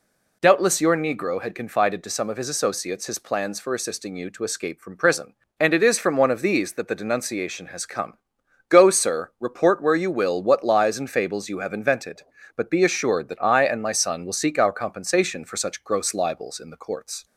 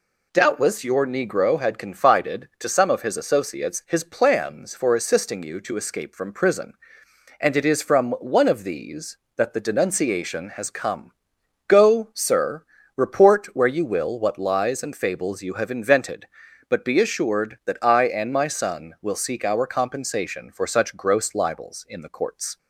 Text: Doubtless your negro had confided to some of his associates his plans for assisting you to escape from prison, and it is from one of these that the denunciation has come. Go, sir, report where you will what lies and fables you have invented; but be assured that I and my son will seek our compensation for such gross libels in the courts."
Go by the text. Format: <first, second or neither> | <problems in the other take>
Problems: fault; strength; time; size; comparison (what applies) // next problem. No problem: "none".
neither | none